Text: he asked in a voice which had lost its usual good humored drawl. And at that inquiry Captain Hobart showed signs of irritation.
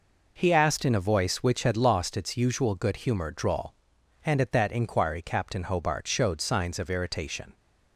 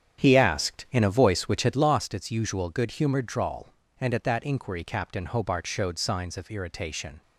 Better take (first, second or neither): first